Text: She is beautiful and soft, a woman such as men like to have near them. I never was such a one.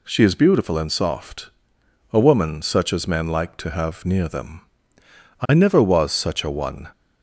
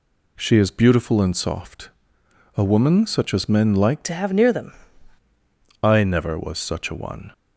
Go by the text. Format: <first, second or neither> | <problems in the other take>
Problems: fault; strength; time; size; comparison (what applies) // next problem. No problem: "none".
first | changes voice from "to" to "them"; from 4.0 to 4.7 s; 0.7 s long